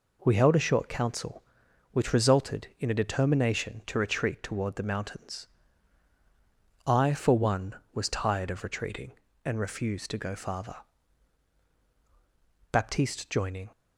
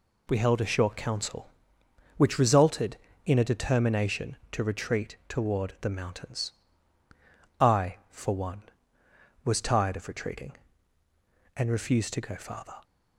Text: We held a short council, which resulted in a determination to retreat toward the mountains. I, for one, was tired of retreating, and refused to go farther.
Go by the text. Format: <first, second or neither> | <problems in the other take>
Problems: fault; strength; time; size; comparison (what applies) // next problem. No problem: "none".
second | goes on to say "Baptiste joining"; noticeable; from 12.7 s on; 1.0 s long